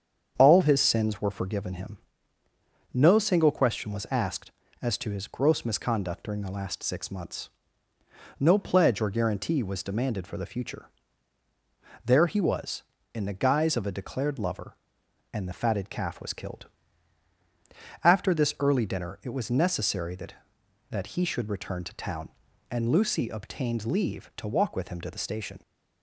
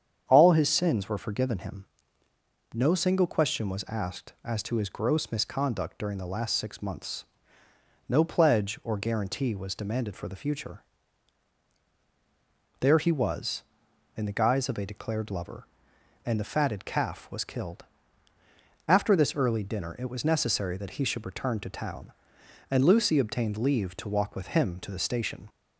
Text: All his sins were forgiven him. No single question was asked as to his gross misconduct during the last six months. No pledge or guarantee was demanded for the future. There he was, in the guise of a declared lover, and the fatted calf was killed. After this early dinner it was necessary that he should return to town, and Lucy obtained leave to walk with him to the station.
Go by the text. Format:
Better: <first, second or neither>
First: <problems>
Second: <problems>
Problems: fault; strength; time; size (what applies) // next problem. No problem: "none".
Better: second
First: starts louder than the rest; strong; until 1.3 s; 7.5 dB // says "that" twice; at 20.8 s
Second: starts louder than the rest; strong; until 1.2 s; 8 dB